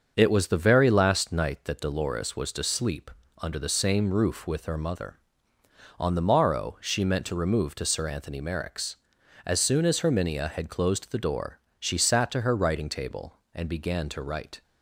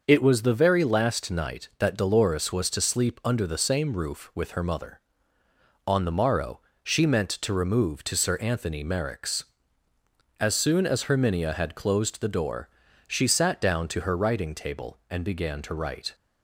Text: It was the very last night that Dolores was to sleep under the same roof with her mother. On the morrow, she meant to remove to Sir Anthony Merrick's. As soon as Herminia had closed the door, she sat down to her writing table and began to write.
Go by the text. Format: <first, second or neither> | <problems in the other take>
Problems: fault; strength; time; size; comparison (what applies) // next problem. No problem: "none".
second | starts louder than the rest; until 1.1 s; 6.5 dB // pauses between "sleep" and "under"; slight; at 3.0 s; 0.32 s long // skips "down"; at 12.3 s